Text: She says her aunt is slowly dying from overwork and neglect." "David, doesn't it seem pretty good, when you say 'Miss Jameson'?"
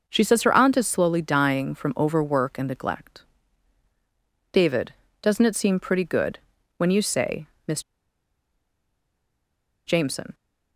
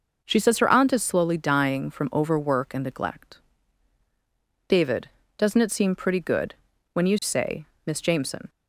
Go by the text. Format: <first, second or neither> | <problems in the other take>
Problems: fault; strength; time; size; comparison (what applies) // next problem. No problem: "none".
second | pauses between "say" and "Miss"; slight; at 7.4 s; 0.18 s long; slight in the second // pauses between "Miss" and "Jameson"; strong; at 7.8 s; 2.0 s long